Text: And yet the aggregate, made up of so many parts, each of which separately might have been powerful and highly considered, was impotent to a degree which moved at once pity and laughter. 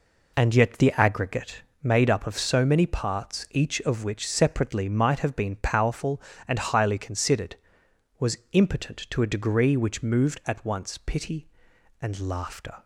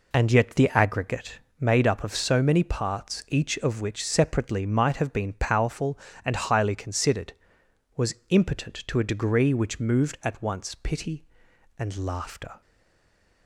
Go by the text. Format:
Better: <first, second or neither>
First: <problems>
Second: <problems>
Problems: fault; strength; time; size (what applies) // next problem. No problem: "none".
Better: first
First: none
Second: stays silent after the last word; slight; from 12.6 s on; 0.8 s long